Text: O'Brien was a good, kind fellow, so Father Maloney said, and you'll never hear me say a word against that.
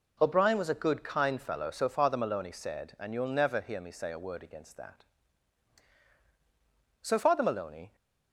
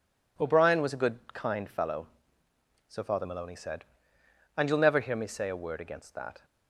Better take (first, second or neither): second